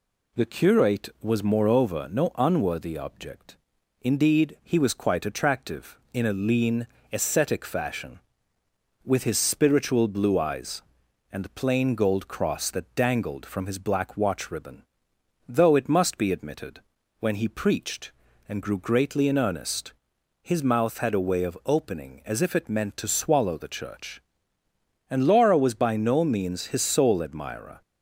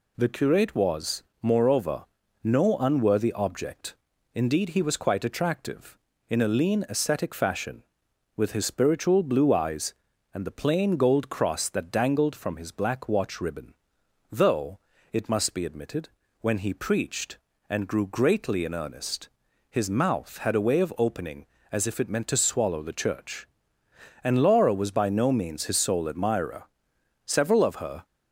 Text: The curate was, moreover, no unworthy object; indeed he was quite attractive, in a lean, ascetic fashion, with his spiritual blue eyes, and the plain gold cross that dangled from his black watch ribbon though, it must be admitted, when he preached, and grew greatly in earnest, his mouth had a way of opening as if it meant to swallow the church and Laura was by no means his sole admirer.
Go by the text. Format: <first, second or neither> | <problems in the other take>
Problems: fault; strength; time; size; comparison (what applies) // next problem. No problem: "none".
first | pauses between "ribbon" and "though"; noticeable; at 13.7 s; 0.58 s long; noticeable in the first // goes on to say "Several of her"; noticeable; from 27.2 s on; 0.80 s long